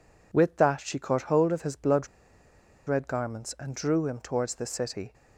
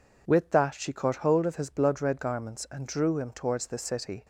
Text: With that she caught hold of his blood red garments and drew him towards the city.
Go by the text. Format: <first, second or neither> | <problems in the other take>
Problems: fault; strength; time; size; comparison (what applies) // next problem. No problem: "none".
second | pauses between "blood" and "red"; noticeable; at 2.0 s; 0.79 s long